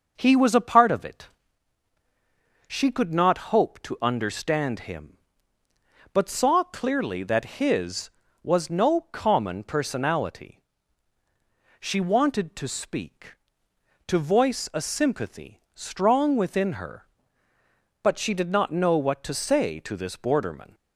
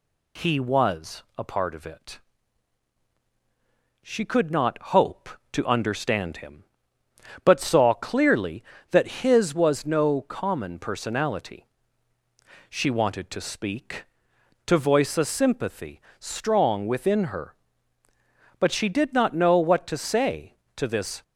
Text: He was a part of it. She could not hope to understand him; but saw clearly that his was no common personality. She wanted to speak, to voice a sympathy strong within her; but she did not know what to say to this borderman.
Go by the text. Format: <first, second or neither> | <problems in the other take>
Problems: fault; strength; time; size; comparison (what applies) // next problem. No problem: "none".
first | pauses between "was" and "a"; slight; at 1.2 s; 0.16 s long // pauses between "not" and "hope"; slight; at 4.7 s; 0.16 s long // pauses between "sympathy" and "strong"; slight; at 16.0 s; 0.16 s long // stops before "borderman"; at 21.2 s